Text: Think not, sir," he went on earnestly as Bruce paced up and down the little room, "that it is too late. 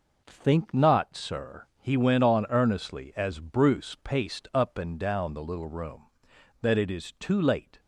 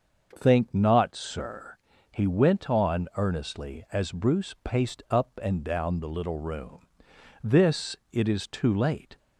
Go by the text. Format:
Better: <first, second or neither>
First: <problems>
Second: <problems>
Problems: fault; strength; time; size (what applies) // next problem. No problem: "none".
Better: first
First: none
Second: starts louder than the rest; noticeable; until 1.3 s; 6 dB // says "this" for "that"; at 7.4 s